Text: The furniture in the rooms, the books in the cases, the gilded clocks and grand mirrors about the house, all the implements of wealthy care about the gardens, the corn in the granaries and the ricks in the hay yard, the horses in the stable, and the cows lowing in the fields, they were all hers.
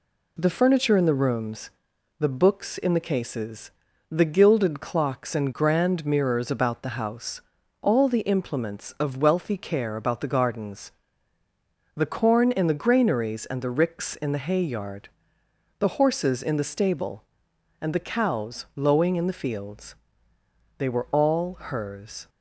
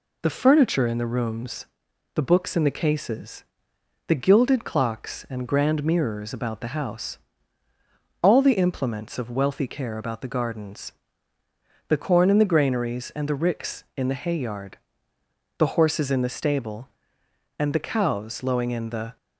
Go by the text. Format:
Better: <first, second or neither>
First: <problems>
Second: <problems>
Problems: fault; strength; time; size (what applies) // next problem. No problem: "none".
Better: first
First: none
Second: stops before "fields they were all hers"; at 19.1 s